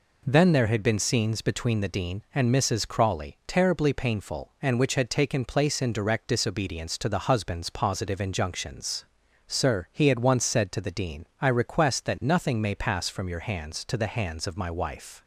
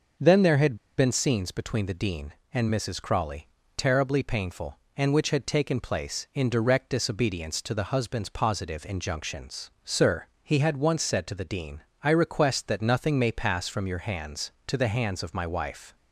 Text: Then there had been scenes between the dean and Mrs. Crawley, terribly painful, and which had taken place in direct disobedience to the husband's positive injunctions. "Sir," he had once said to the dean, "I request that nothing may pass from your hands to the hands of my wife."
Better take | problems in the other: first | pauses between "had" and "been"; slight; at 0.7 s; 0.22 s long

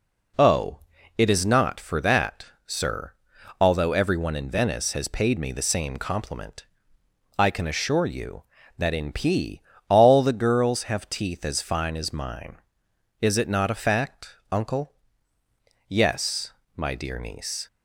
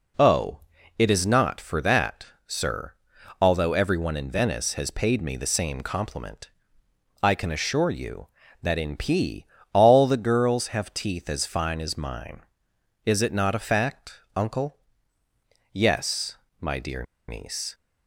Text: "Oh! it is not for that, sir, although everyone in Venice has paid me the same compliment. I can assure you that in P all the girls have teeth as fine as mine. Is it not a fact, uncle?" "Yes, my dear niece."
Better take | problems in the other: first | pauses between "P" and "all"; slight; at 9.4 s; 0.28 s long; slight in the first // pauses between "dear" and "niece"; slight; at 17.0 s; 0.25 s long

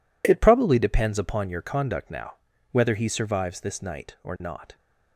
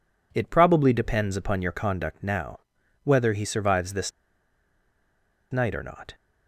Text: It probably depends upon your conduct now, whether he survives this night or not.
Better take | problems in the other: first | pauses between "this" and "night"; strong; at 4.1 s; 1.4 s long

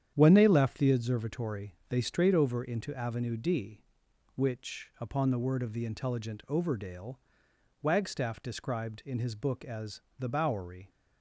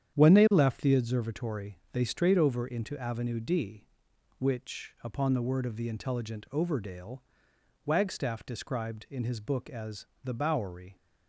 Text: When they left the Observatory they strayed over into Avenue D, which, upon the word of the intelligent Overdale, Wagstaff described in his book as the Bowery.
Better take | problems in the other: neither | starts louder than the rest; strong; the same in both // pauses between "Observatory" and "they"; slight; the same in both // pauses between "as" and "the"; slight; the same in both

